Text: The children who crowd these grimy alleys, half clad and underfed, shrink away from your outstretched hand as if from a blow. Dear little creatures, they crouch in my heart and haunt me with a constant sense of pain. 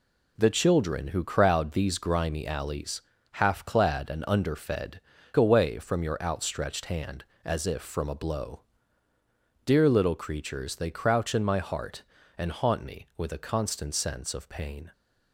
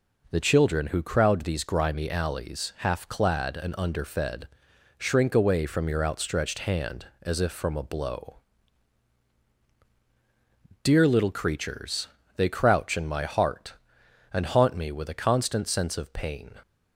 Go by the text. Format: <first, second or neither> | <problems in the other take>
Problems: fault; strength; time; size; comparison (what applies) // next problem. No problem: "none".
second | skips "shrink"; at 5.1 s